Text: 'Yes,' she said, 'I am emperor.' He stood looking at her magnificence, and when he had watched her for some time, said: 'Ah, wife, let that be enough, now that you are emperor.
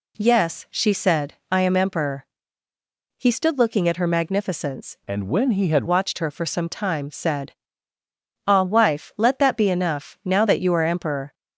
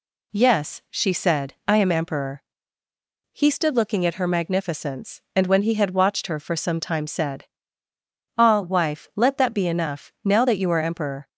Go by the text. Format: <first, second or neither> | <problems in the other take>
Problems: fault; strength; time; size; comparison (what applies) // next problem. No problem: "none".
second | changes voice from "and" to "had"; from 5.0 to 5.8 s; 0.8 s long